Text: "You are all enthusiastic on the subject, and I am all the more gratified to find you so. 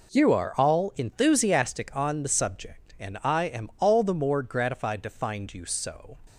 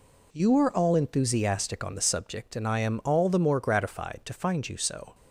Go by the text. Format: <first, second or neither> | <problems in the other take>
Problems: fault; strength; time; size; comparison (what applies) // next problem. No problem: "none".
neither | none